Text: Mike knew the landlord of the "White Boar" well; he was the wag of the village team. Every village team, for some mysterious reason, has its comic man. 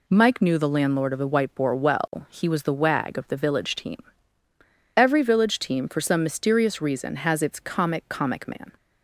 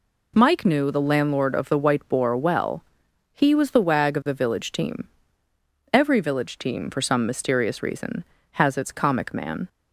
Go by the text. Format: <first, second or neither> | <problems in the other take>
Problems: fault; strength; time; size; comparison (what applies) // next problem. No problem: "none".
second | says "comic" twice; at 8.0 s